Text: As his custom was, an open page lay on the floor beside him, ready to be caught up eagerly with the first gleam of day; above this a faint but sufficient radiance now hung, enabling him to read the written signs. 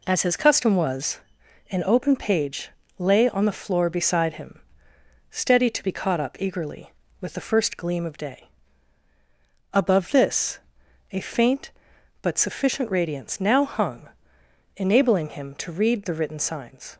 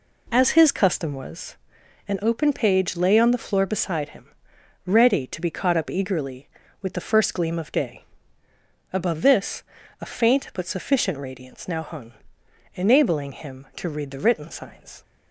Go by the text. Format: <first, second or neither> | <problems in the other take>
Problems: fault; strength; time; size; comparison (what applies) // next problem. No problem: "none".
second | pauses between "page" and "lay"; slight; at 2.7 s; 0.28 s long // says "steady" for "ready"; at 5.3 s // pauses between "this" and "a"; noticeable; at 10.5 s; 0.54 s long; also in the second